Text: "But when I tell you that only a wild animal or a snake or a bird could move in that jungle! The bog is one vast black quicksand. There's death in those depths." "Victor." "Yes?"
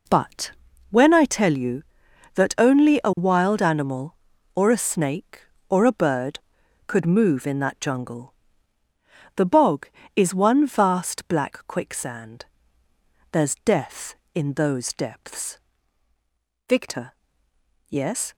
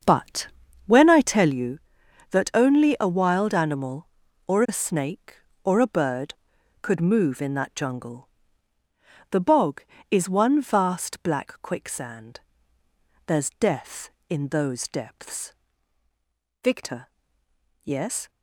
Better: first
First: pauses between "But" and "when"; at 0.5 s; 0.38 s long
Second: starts louder than the rest; until 1.6 s; 6.5 dB // pauses between "But" and "when"; at 0.4 s; 0.38 s long

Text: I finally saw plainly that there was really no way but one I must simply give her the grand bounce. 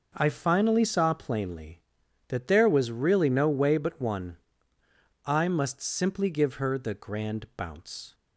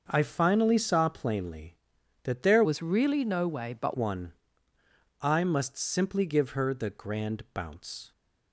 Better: first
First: pauses between "one" and "I"; noticeable; at 4.3 s; 0.90 s long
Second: starts louder than the rest; until 1.0 s; 6 dB // changes voice from "was" to "but"; from 2.6 to 3.9 s; 1.3 s long // pauses between "one" and "I"; noticeable; at 4.3 s; 0.90 s long

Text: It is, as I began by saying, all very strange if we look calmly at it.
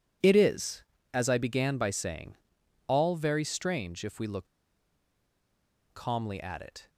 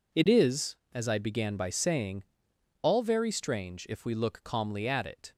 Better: second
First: pauses between "look" and "calmly"; strong; at 4.4 s; 1.5 s long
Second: none

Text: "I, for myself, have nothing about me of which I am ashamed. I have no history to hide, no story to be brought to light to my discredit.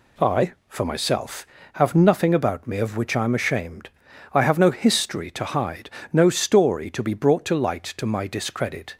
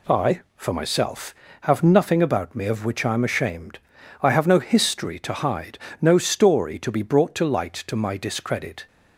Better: neither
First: none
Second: none

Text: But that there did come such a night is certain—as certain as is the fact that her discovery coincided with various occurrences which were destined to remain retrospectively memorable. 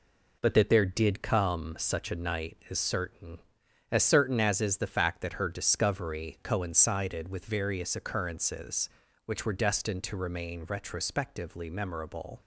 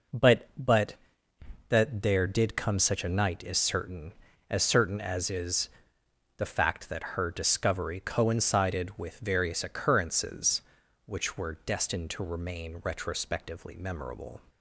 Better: first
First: none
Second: says "But" twice; at 0.5 s // pauses between "is" and "the"; noticeable; at 5.6 s; 0.68 s long

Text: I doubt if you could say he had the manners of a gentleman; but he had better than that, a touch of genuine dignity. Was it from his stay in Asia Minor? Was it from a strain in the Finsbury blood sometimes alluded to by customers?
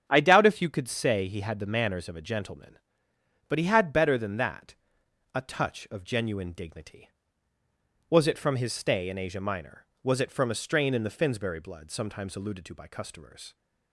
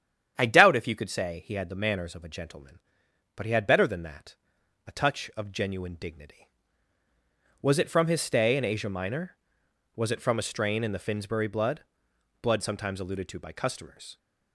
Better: first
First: starts louder than the rest; strong; until 1.0 s; 8.5 dB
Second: starts louder than the rest; strong; until 1.3 s; 9 dB // says "blood" twice; at 12.4 s

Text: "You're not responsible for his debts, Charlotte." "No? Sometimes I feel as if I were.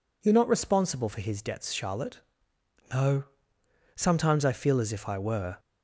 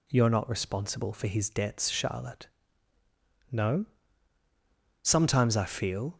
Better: first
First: none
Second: stops before "as if I were"; at 6.1 s

